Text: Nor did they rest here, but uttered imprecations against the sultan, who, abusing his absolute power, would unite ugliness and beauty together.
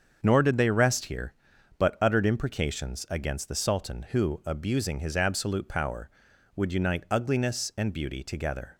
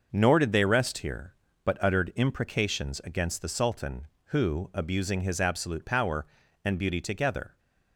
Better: first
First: starts louder than the rest; until 1.2 s; 7 dB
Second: starts louder than the rest; noticeable; until 1.1 s; 6 dB // skips "would unite ugliness"; at 6.4 s

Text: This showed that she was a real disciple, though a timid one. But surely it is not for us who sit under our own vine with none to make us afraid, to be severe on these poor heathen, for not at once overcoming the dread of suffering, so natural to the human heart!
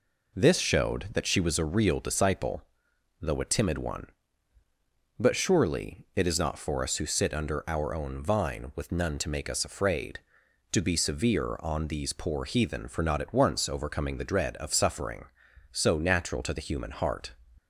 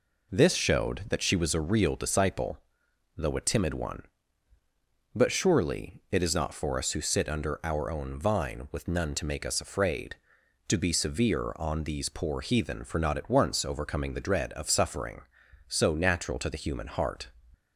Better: neither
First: none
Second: none

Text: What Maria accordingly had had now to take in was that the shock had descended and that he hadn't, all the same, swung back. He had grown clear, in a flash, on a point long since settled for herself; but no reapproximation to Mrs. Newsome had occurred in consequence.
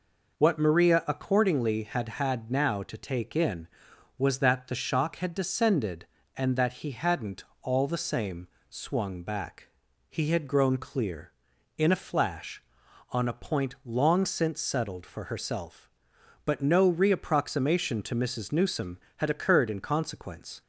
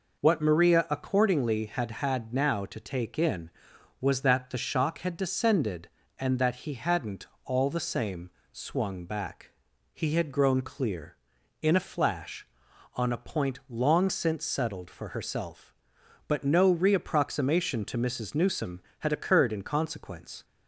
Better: neither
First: none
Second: none

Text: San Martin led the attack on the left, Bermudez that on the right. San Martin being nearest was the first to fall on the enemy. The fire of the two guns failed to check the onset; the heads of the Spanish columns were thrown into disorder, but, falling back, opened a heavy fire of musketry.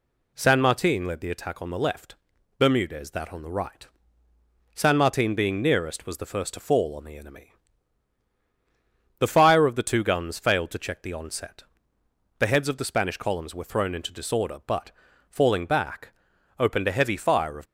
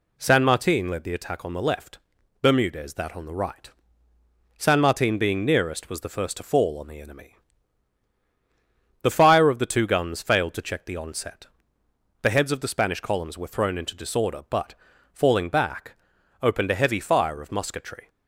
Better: second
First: stops before "musketry"; at 17.6 s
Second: none

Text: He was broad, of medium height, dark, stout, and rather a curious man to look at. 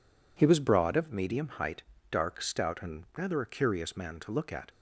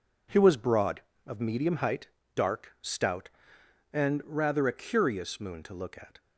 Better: first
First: none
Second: says "moon" for "man"; at 5.3 s

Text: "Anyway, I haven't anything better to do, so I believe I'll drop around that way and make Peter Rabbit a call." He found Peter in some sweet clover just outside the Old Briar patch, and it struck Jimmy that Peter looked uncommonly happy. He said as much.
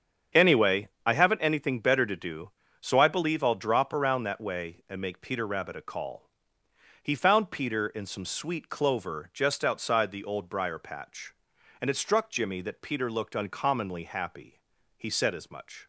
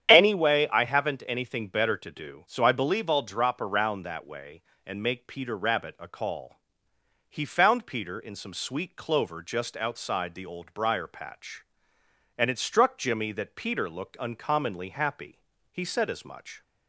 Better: neither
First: starts louder than the rest; strong; until 1.5 s; 8 dB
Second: starts louder than the rest; strong; until 1.1 s; 9 dB

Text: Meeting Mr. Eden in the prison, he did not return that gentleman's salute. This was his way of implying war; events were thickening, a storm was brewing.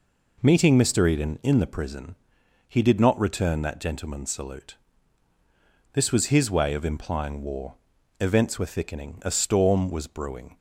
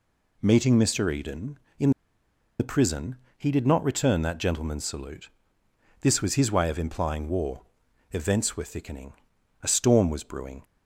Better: first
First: none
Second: pauses between "in" and "the"; noticeable; at 1.9 s; 0.69 s long

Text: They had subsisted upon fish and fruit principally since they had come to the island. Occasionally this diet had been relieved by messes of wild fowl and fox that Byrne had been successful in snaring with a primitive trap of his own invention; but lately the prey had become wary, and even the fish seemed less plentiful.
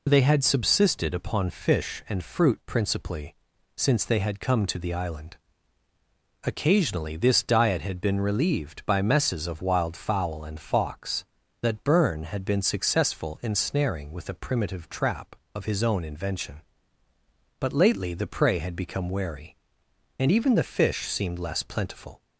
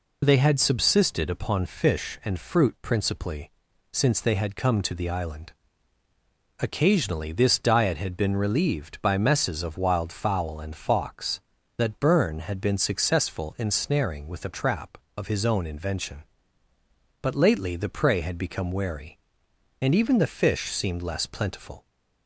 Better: first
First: pauses between "principally" and "since"; at 3.3 s; 0.40 s long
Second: pauses between "principally" and "since"; at 3.5 s; 0.40 s long // skips "primitive"; at 14.5 s

